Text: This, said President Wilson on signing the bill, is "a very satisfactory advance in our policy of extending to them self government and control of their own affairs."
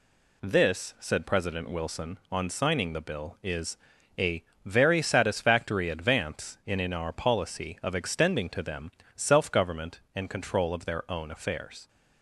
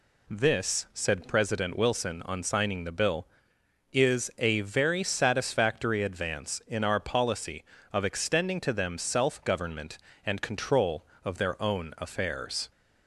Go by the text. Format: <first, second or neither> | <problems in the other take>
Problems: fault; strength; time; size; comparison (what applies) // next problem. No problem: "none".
second | pauses between "is" and "a"; at 3.7 s; 0.44 s long // pauses between "a" and "very"; slight; at 4.4 s; 0.20 s long // says "in" twice; at 6.7 s // pauses between "them" and "self"; slight; at 8.9 s; 0.24 s long